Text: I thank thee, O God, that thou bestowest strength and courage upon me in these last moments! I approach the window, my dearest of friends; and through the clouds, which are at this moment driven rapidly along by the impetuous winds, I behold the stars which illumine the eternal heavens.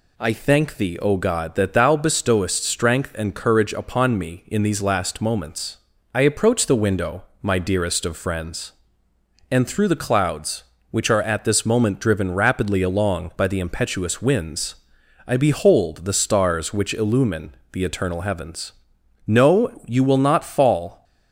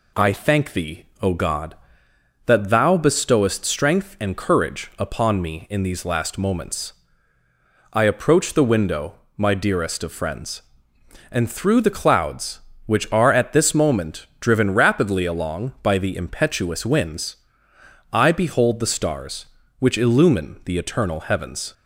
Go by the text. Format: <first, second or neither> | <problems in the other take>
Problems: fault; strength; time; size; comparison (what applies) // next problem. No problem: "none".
second | pauses between "illumine" and "the"; slight; at 17.5 s; 0.20 s long // goes on to say "No you will not fall"; strong; from 19.2 s on; 1.7 s long